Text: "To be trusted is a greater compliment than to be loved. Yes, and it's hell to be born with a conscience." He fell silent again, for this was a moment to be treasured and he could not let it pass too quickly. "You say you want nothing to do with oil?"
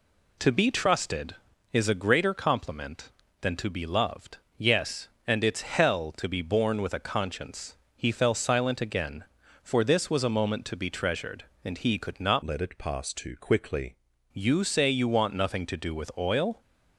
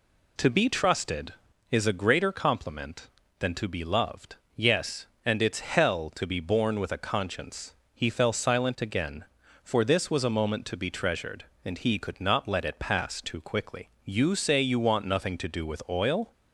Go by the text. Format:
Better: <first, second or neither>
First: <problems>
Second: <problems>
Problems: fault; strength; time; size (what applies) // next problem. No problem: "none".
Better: second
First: changes voice from "let" to "quickly"; from 12.4 to 13.9 s; 1.5 s long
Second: none